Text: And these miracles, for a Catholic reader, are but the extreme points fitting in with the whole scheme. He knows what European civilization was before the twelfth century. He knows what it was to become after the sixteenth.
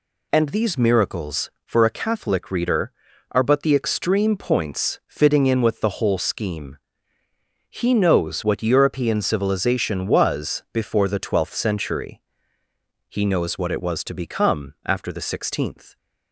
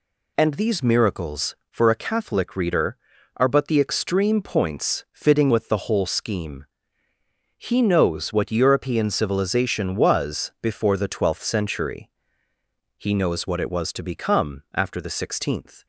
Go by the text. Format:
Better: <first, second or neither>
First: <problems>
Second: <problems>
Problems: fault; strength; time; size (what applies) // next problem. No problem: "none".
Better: first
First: none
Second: skips "in"; at 5.5 s